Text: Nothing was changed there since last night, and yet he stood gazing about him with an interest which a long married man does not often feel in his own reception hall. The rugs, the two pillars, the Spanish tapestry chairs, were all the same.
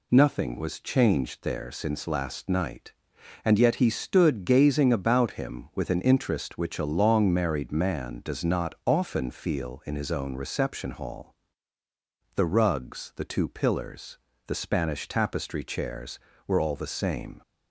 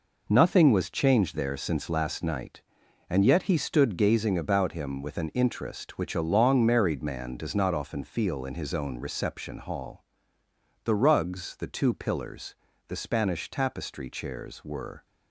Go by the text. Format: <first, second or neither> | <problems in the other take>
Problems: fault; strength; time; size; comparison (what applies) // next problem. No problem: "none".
first | stops before "all the same"; at 15.0 s